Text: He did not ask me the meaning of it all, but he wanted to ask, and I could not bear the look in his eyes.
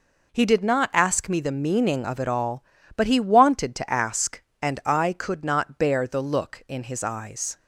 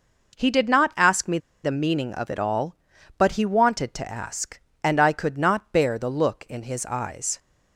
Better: first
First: none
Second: pauses between "me" and "the"; slight; at 1.3 s; 0.25 s long

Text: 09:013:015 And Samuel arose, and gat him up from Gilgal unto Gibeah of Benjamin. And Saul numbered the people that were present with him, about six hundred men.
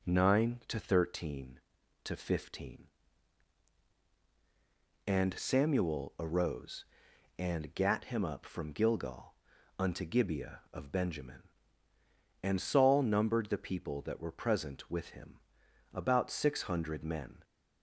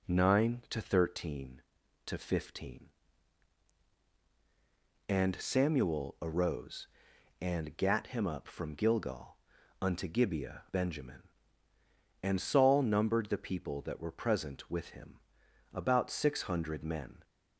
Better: first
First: pauses between "Gilgal" and "unto"; at 9.3 s; 0.42 s long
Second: pauses between "Gilgal" and "unto"; at 9.3 s; 0.42 s long // skips "of"; at 10.6 s

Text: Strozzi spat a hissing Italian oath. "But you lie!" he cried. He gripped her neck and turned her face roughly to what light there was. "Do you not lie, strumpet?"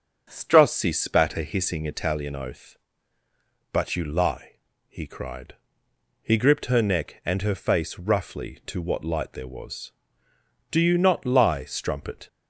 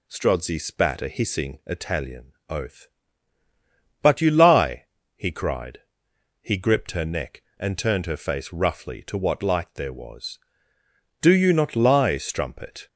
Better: second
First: starts louder than the rest; until 1.3 s; 7 dB // skips "turned"; at 7.4 s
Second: none

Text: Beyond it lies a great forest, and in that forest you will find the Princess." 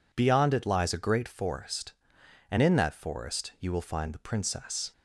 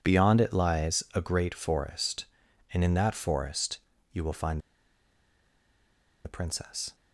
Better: first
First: none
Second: pauses between "forest" and "you"; slight; at 3.7 s; 0.36 s long // pauses between "find" and "the"; strong; at 4.5 s; 1.6 s long

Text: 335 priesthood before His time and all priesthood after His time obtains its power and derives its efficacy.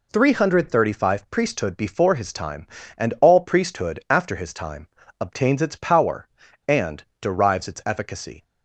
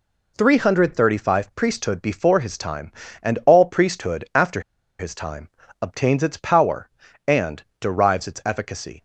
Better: first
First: pauses between "time" and "obtains"; slight; at 4.8 s; 0.34 s long // pauses between "and" and "derives"; slight; at 7.0 s; 0.16 s long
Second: pauses between "after" and "His"; at 4.6 s; 0.37 s long // pauses between "time" and "obtains"; slight; at 5.4 s; 0.34 s long // pauses between "and" and "derives"; slight; at 7.6 s; 0.16 s long

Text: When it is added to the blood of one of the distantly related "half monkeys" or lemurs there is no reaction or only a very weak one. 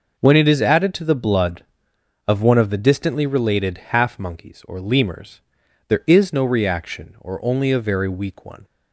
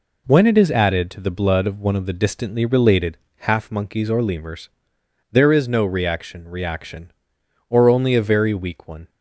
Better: first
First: pauses between "lemurs" and "there"; noticeable; at 5.4 s; 0.46 s long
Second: pauses between "related" and "half"; slight; at 3.1 s; 0.22 s long // pauses between "lemurs" and "there"; noticeable; at 4.6 s; 0.64 s long // says "reaction" twice; at 6.4 s

